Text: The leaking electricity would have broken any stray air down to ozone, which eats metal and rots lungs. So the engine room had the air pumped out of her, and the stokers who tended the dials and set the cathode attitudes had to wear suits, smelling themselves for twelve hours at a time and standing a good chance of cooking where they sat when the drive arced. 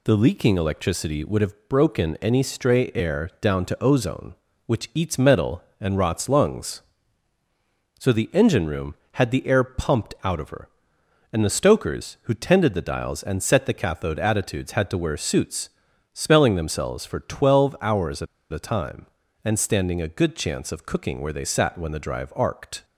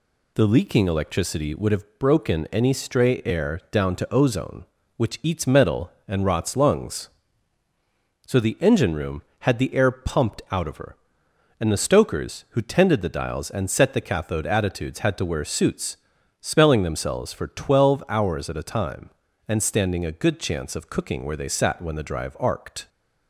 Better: second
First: pauses between "at" and "a"; slight; at 18.2 s; 0.26 s long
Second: none

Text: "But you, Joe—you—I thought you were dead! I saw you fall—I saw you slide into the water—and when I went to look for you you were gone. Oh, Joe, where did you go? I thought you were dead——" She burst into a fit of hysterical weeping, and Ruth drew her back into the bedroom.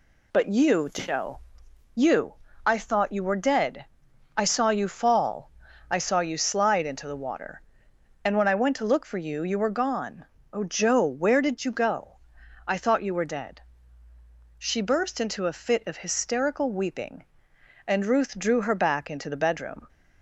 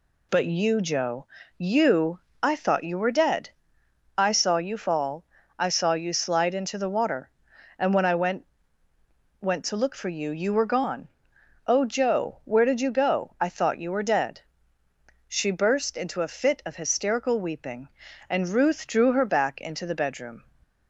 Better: first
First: none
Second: says "went" twice; at 9.3 s

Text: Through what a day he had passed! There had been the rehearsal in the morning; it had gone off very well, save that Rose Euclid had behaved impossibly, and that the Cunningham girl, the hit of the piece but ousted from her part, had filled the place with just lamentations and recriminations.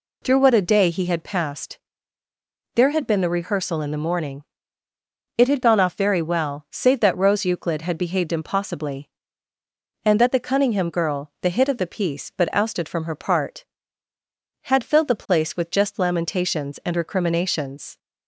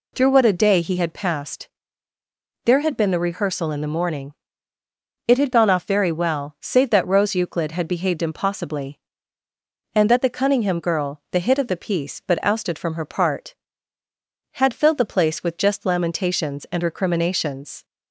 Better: neither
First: none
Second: none

